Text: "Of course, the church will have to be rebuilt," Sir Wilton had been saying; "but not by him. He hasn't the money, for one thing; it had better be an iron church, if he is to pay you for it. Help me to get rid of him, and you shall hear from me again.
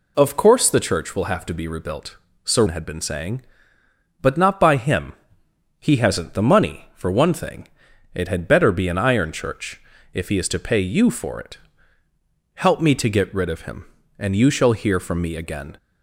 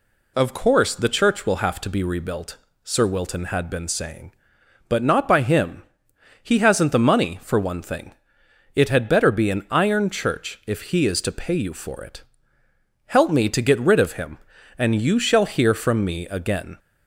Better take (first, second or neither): second